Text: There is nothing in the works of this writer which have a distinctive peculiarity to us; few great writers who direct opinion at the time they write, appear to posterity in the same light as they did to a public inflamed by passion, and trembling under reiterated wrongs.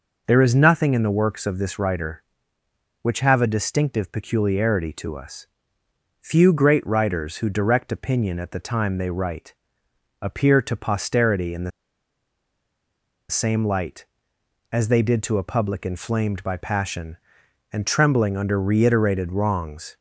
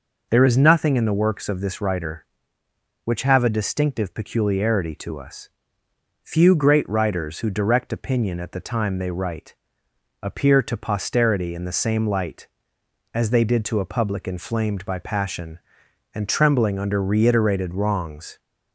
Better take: second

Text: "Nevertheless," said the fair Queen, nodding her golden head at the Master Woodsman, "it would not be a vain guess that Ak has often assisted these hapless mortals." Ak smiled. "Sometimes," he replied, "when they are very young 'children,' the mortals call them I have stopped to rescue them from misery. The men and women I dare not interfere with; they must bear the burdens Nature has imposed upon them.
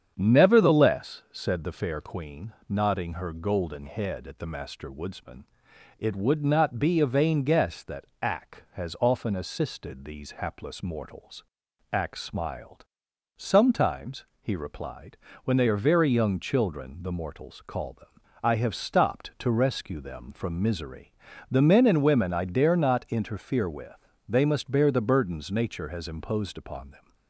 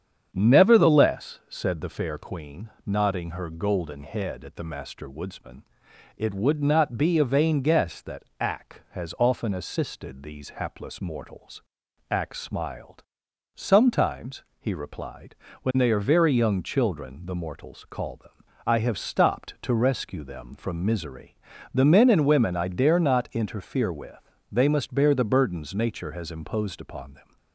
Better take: neither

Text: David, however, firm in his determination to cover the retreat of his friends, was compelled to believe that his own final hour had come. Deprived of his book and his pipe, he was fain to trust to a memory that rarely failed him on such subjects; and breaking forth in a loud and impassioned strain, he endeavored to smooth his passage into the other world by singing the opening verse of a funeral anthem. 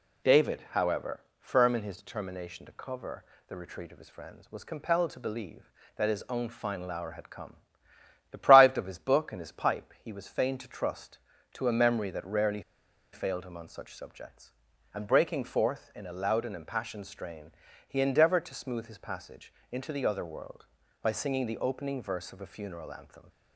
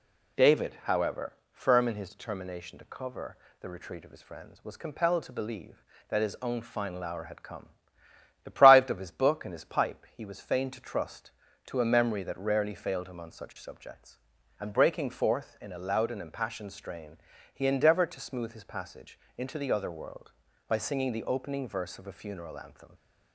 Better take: second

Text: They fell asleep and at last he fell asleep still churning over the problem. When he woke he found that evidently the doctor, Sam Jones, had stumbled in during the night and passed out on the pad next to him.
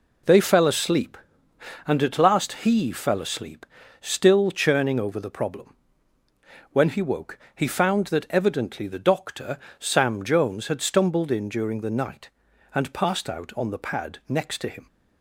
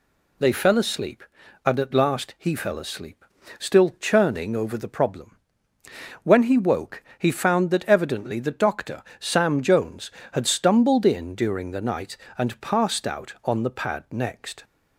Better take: first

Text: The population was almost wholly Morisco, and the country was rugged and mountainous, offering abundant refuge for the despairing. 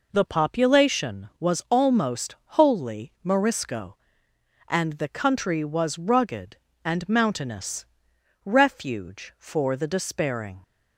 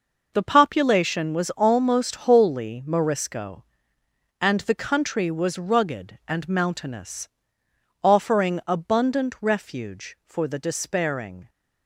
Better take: second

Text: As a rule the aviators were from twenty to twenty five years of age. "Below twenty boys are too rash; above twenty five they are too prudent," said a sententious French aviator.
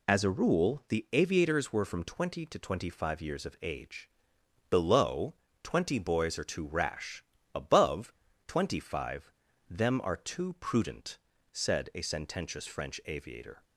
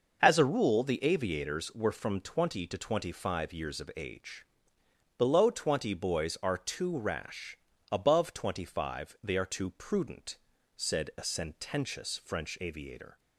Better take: second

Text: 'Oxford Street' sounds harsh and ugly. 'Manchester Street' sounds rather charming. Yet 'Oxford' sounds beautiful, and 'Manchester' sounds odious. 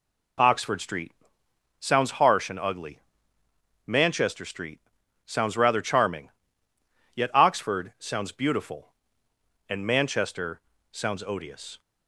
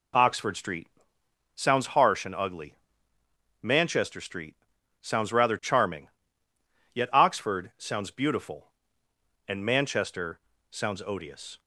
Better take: neither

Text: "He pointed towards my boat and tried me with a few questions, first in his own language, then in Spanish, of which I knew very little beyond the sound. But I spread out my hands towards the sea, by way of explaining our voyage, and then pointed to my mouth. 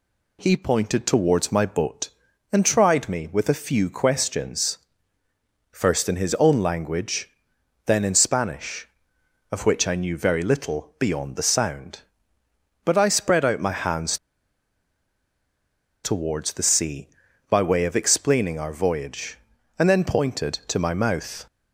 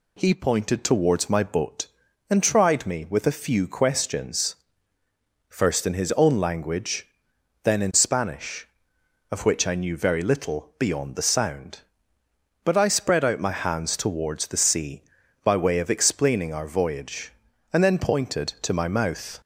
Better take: second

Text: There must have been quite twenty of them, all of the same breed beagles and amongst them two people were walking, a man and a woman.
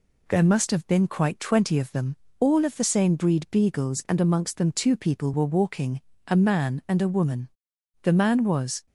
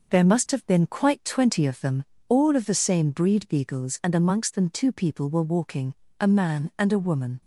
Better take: second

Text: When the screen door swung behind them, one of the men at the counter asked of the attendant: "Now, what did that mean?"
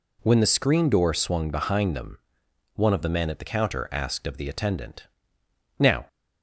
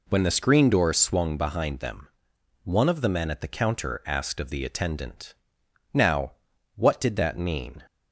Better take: second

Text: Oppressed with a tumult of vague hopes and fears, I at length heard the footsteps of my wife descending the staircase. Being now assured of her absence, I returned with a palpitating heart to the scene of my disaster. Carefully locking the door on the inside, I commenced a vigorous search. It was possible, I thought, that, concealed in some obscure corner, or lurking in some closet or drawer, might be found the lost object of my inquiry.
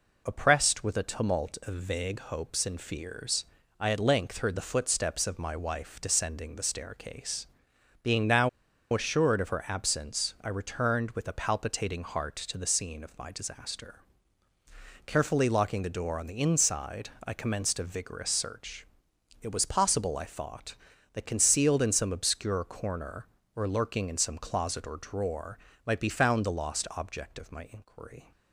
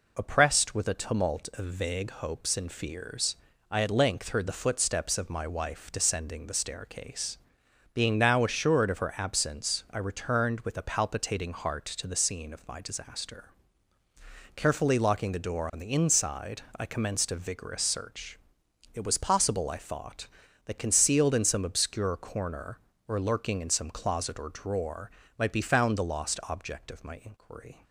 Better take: second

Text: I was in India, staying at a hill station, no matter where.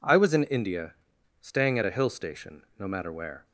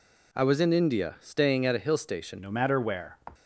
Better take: first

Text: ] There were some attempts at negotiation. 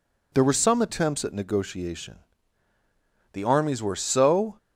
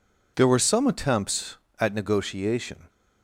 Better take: second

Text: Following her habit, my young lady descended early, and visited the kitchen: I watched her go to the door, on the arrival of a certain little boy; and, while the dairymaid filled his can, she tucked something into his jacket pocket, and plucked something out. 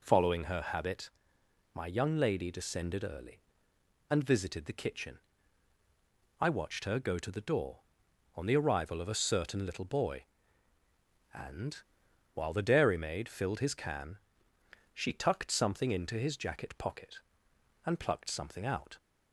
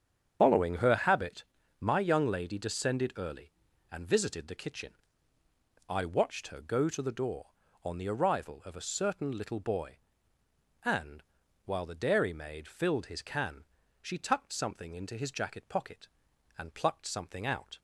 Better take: first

